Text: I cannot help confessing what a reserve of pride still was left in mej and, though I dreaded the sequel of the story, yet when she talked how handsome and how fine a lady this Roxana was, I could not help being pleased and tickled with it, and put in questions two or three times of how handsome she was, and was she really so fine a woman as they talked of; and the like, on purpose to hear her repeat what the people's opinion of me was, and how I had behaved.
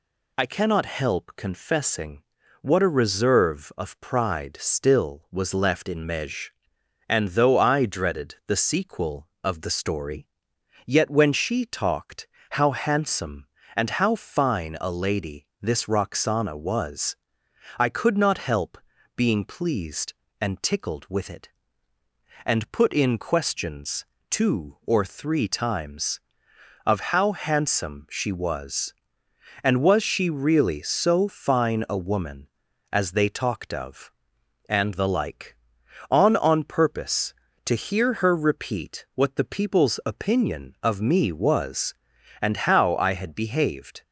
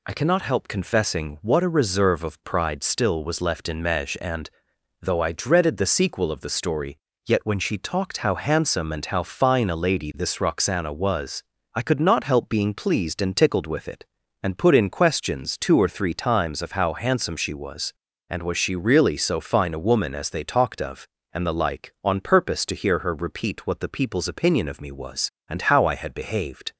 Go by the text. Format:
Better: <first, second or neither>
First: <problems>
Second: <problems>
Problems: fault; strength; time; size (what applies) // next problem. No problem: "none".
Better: second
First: pauses between "confessing" and "what"; at 2.2 s; 0.38 s long // pauses between "talked" and "how"; slight; at 12.2 s; 0.24 s long // pauses between "help" and "being"; at 18.7 s; 0.38 s long // pauses between "questions" and "two"; slight; at 24.0 s; 0.26 s long // says "on" twice; at 36.3 s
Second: none